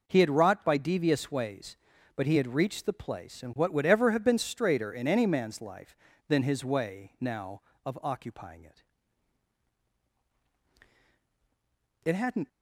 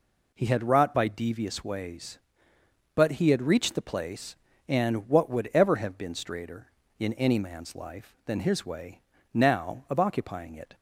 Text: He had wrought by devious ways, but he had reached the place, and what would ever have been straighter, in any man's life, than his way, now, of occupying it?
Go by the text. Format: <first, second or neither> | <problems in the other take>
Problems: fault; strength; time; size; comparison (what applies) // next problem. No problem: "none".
second | goes on to say "It hadn't"; slight; from 12.0 s on; 0.44 s long